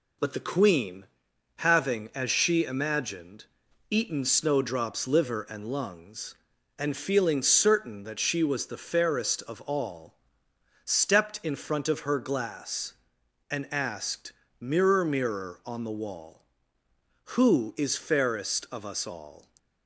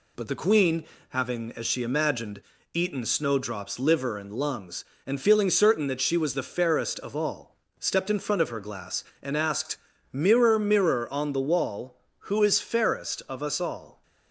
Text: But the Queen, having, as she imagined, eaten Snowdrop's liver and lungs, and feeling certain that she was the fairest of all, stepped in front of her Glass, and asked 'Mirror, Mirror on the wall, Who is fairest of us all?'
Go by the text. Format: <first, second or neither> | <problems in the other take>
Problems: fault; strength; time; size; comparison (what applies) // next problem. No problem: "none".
neither | pauses between "asked" and "Mirror"; slight; the same in both